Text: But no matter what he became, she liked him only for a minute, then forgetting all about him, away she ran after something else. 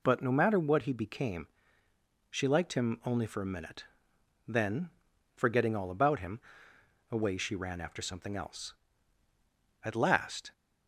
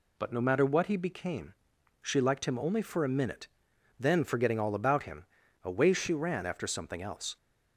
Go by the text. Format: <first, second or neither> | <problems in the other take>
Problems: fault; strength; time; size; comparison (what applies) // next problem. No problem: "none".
second | pauses between "then" and "forgetting"; noticeable; at 4.8 s; 0.46 s long // goes on to say "At last"; noticeable; from 9.8 s on; 0.68 s long